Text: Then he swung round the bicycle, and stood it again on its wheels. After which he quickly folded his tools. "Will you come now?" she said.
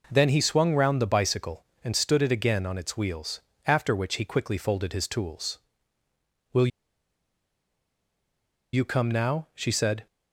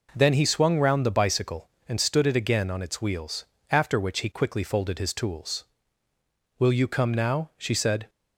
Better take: second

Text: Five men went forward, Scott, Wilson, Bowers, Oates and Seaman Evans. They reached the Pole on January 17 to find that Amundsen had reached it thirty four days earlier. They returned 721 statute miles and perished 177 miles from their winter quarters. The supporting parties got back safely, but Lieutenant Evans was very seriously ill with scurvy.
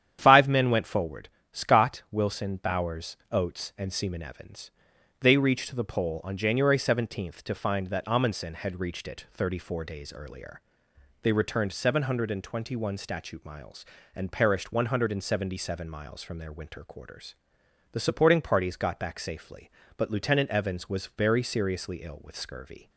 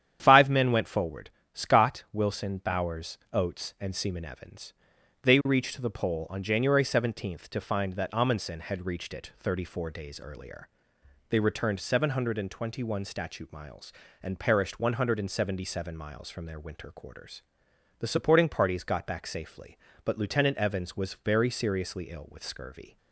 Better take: neither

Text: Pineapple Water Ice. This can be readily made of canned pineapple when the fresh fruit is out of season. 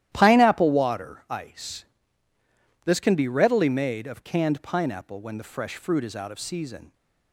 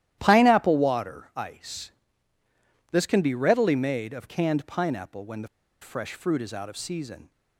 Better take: first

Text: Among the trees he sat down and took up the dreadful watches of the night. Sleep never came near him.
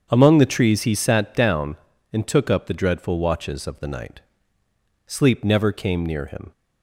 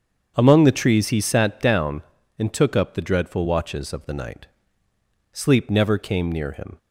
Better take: neither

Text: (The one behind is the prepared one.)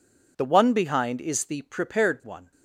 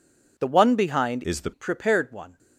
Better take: first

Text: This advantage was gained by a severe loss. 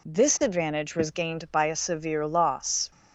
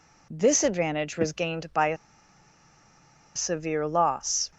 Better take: first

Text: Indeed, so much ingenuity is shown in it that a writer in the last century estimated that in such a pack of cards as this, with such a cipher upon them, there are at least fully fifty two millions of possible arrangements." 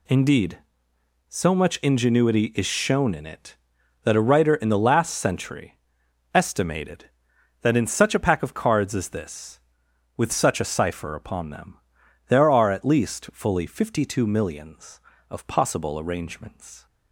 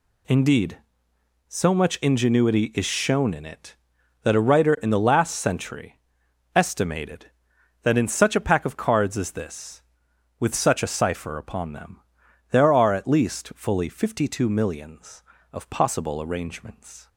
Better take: neither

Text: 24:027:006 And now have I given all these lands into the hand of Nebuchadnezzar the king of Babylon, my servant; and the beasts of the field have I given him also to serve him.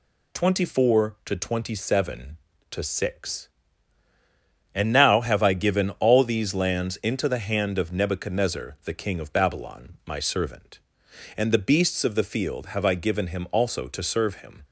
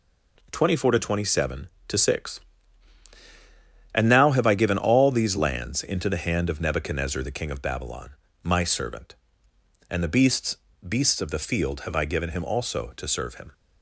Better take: first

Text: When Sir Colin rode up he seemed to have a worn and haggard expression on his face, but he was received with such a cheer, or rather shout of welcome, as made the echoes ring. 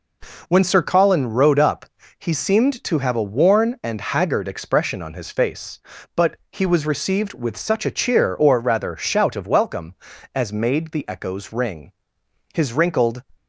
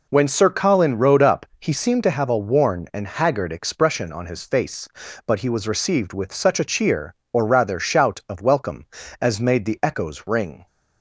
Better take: second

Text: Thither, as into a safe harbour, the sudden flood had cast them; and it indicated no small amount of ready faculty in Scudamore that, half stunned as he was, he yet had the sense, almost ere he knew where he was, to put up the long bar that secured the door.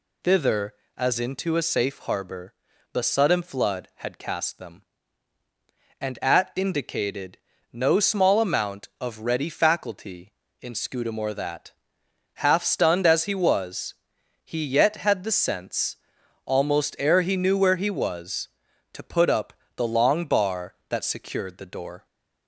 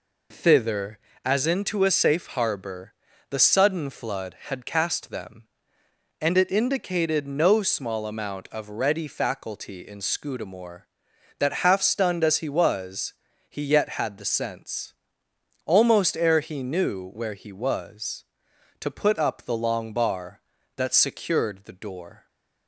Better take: second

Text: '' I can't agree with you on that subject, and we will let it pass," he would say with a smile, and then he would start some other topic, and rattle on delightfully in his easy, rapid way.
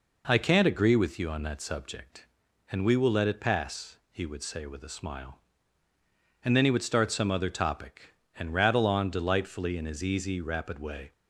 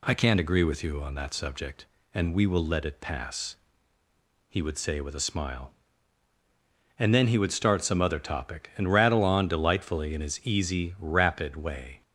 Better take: neither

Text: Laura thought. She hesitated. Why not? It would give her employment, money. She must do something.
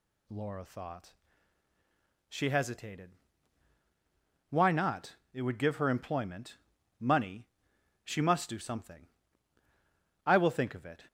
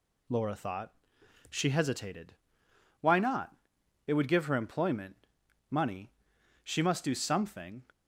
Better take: second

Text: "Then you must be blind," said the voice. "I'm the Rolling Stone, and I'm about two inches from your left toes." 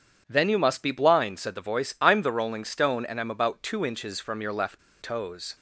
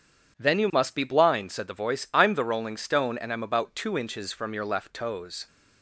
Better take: second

